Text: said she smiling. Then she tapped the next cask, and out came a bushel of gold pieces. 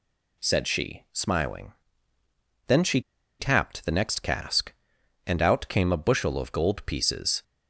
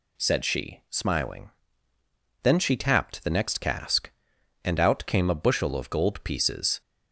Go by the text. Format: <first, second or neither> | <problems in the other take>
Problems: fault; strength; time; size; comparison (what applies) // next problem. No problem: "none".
second | pauses between "she" and "tapped"; at 2.9 s; 0.39 s long